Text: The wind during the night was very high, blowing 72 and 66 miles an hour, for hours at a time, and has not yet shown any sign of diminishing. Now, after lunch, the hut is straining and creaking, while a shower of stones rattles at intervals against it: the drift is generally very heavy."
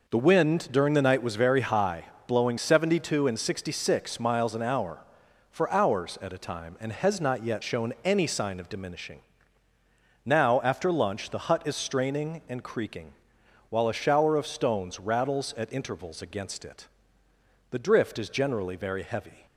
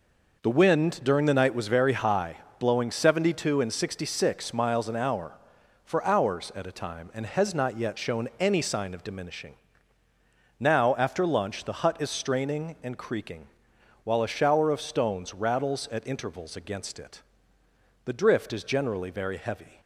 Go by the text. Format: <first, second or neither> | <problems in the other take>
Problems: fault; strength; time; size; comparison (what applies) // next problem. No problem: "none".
neither | none